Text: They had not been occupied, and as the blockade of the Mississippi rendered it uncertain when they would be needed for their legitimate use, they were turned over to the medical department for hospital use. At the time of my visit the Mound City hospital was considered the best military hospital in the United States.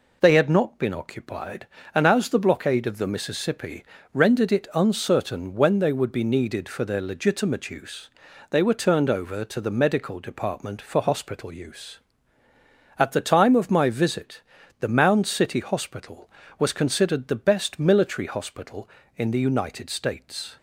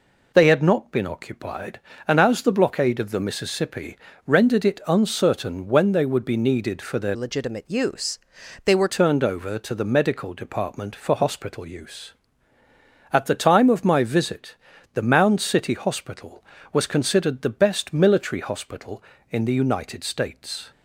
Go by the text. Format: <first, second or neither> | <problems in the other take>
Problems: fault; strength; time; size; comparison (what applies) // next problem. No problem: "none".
first | pauses between "Mississippi" and "rendered"; slight; at 3.9 s; 0.30 s long; slight in the first // changes voice from "legitimate" to "were"; from 7.1 to 8.8 s; 1.7 s long // pauses between "visit" and "the"; at 14.5 s; 0.38 s long; also in the first